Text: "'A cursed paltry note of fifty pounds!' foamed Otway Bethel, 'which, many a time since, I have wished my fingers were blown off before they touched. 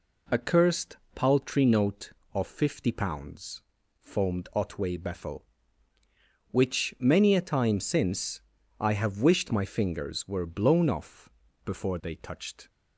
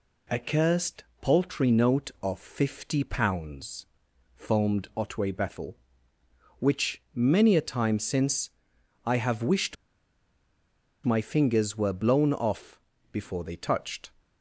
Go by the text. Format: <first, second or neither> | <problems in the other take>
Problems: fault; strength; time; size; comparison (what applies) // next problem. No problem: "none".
first | pauses between "cursed" and "paltry"; slight; at 1.0 s; 0.18 s long; slight in the first // pauses between "wished" and "my"; strong; at 9.7 s; 1.3 s long // pauses between "off" and "before"; slight; at 12.7 s; 0.32 s long; slight in the first